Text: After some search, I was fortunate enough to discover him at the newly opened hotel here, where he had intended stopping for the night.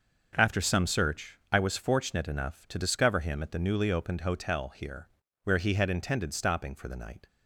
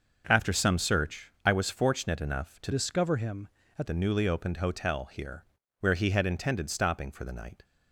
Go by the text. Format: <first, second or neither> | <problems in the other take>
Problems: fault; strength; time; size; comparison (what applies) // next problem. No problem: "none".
first | changes voice from "discover" to "at"; from 2.7 to 3.8 s; 1.1 s long